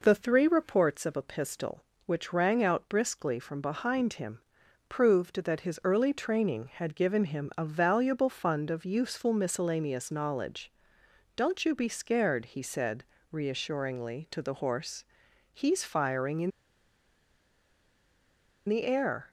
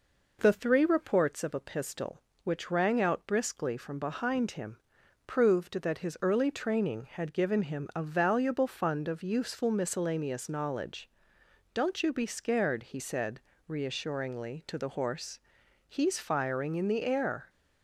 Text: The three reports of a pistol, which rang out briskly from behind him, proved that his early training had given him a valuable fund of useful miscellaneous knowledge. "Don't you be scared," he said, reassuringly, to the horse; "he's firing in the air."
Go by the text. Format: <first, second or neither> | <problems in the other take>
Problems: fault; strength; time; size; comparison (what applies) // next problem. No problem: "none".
second | pauses between "in" and "the"; strong; at 16.5 s; 2.1 s long